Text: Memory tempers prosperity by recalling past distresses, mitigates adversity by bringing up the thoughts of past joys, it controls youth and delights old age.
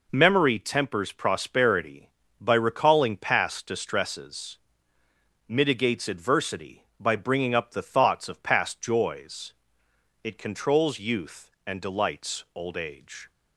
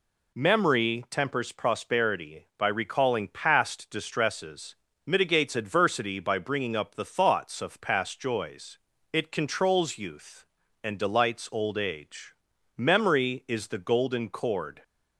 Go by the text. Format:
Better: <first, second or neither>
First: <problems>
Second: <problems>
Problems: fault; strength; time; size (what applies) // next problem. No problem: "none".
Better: first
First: none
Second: goes on to say "Memory is the golden cord"; strong; from 12.7 s on; 2.0 s long